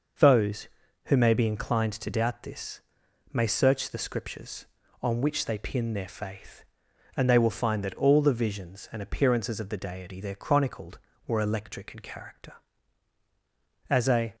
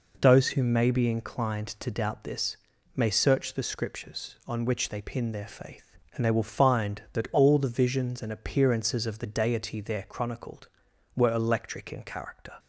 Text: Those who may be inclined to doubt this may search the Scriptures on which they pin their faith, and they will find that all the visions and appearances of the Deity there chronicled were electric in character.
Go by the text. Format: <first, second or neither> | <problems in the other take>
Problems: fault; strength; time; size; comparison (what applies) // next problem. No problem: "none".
second | pauses between "this" and "may"; noticeable; at 2.8 s; 0.52 s long; also in the second // goes on to say "As a"; slight; from 13.8 s on; 0.46 s long